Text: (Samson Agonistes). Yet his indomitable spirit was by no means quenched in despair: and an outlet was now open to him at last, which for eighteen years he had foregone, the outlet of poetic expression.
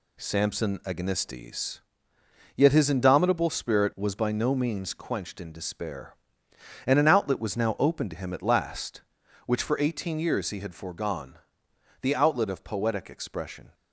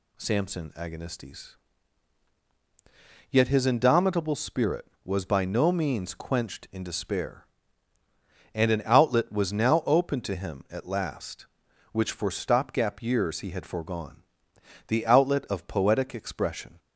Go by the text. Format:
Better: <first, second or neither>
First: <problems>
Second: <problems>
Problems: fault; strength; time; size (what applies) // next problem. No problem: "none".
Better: first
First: none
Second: says "stopgap" for "eighteen"; at 12.3 s